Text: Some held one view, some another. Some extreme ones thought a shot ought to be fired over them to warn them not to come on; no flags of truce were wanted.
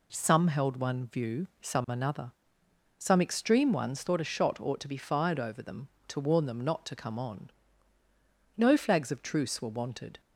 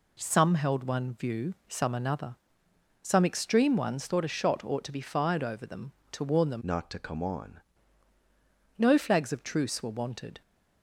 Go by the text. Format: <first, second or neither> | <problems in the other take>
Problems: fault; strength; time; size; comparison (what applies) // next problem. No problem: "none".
first | changes voice from "not" to "on"; from 6.6 to 7.6 s; 1.0 s long